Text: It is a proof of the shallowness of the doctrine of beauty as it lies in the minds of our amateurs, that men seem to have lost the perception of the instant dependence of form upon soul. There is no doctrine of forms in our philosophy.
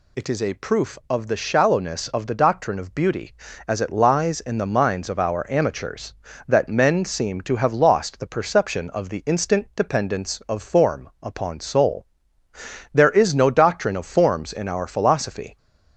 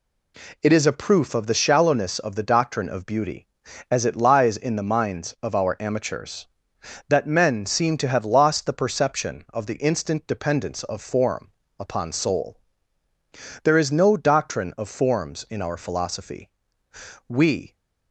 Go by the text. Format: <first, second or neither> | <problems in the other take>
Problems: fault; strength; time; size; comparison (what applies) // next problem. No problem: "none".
first | pauses between "form" and "upon"; slight; at 11.5 s; 0.30 s long // goes on to say "We"; slight; from 17.2 s on; 0.48 s long